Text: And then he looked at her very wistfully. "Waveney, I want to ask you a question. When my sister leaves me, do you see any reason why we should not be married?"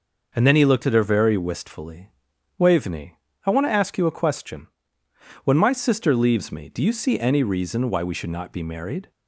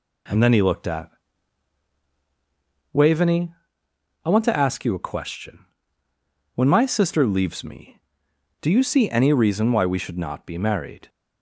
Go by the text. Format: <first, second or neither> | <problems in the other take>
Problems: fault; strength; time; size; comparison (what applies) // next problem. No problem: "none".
first | skips "her very wistfully"; at 2.0 s